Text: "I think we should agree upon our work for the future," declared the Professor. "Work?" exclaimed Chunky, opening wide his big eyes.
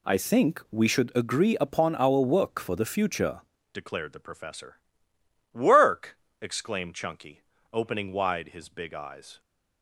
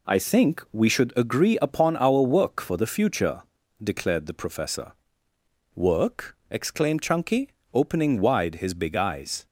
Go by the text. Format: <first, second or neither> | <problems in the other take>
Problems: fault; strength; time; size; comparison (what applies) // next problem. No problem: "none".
second | changes voice at "declared"; from 3.7 s on; 5.7 s long